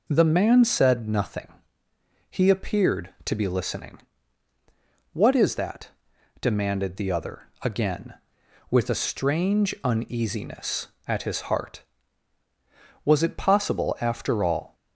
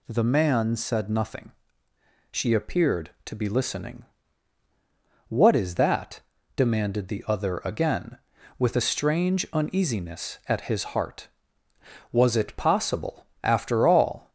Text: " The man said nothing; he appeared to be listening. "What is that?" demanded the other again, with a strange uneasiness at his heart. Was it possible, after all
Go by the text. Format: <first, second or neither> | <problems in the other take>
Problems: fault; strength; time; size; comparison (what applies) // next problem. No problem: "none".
first | says "she" for "he"; at 2.2 s